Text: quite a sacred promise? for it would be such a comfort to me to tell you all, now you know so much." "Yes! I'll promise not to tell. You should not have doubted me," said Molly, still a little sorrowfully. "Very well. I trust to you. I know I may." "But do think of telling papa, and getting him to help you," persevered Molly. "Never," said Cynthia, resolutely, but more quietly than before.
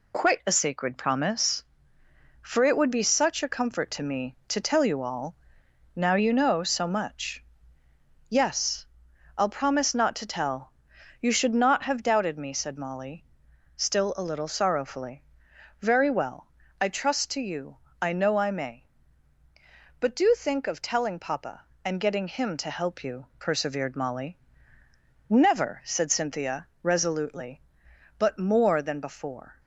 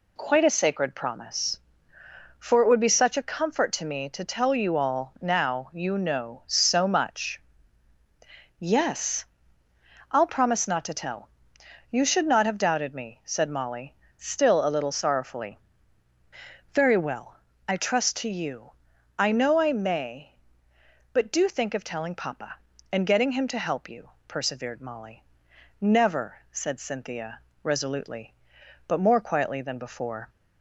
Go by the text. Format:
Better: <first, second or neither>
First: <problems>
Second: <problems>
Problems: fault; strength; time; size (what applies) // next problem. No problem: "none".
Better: second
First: skips "quietly"; at 28.8 s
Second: none